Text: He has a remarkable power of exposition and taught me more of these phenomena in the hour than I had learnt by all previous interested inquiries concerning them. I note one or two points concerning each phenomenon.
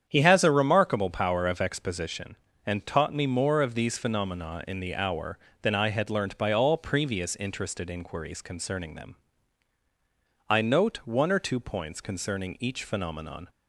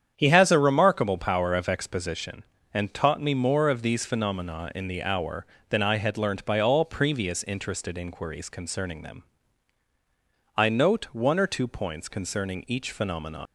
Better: first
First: starts louder than the rest; strong; until 1.1 s; 8.5 dB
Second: starts louder than the rest; strong; until 1.1 s; 8.5 dB // leaves "phenomenon" unfinished; at 13.4 s; 115 ms

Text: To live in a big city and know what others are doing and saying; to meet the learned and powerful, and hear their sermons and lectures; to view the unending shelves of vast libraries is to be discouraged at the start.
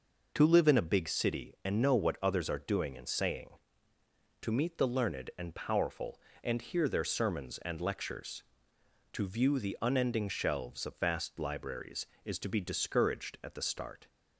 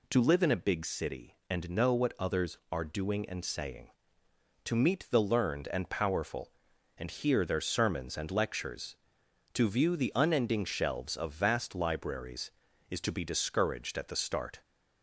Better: neither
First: none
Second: none

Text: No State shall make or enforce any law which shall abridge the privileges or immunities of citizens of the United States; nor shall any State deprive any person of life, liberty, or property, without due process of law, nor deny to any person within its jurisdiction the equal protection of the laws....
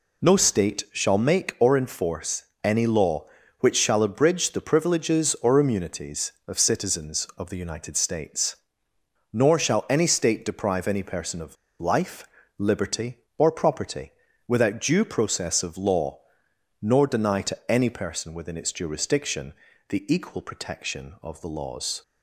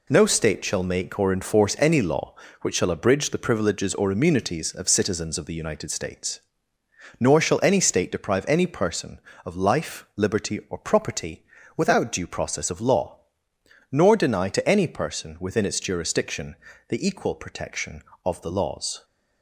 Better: second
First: pauses between "enforce" and "any"; slight; at 2.4 s; 0.18 s long // pauses between "of" and "life"; slight; at 11.5 s; 0.24 s long // pauses between "jurisdiction" and "the"; slight; at 19.5 s; 0.34 s long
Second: pauses between "jurisdiction" and "the"; slight; at 16.5 s; 0.34 s long

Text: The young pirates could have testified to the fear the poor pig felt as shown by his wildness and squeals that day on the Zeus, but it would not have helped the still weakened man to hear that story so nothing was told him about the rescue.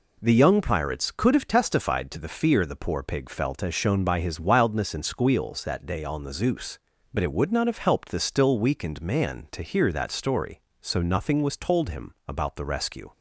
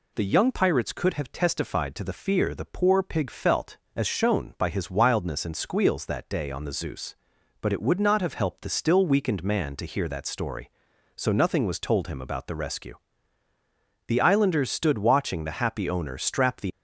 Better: first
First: none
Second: goes on to say "The Islanders stood watching the happy owner strap the"; strong; from 14.0 s on; 2.6 s long

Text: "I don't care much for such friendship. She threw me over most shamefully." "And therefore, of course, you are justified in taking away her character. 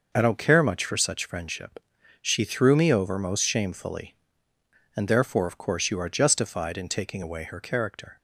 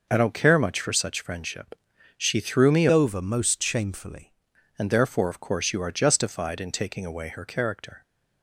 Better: first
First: none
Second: changes voice from "over" to "shamefully"; from 2.9 to 4.3 s; 1.4 s long

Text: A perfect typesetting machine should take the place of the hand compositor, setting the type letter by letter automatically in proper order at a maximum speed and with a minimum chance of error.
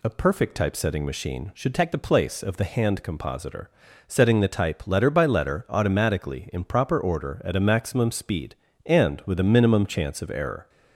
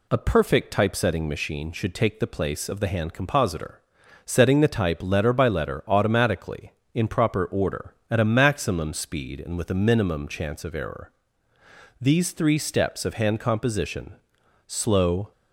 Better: first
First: none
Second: goes on to say "These three steps of hand composition slow"; strong; from 11.9 s on; 3.3 s long

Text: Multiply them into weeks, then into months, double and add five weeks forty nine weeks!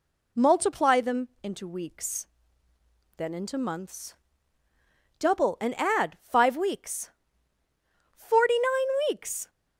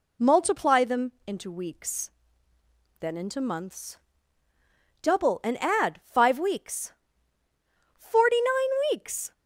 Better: neither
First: pauses between "them" and "into"; slight; at 1.2 s; 0.16 s long // pauses between "weeks" and "forty"; at 7.1 s; 1.0 s long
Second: pauses between "them" and "into"; slight; at 1.0 s; 0.16 s long // pauses between "weeks" and "forty"; at 6.9 s; 1.0 s long

